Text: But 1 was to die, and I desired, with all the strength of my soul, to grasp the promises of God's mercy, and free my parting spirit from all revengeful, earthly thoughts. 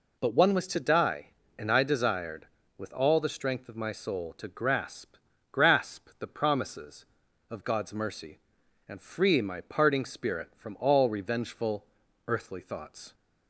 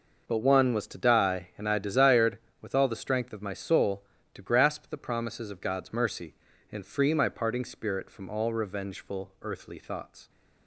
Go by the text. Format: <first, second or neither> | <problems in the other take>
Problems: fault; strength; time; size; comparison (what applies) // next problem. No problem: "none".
second | says "grasp" twice; at 5.5 s